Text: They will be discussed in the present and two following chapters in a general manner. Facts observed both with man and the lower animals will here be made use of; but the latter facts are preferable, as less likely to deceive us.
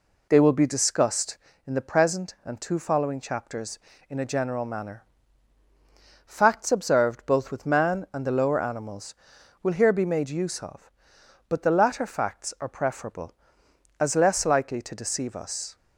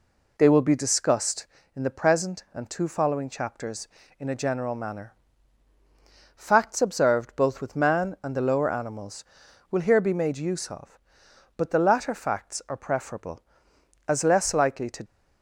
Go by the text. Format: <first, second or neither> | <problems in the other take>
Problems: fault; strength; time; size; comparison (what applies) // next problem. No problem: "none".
first | stops before "deceive us"; at 15.0 s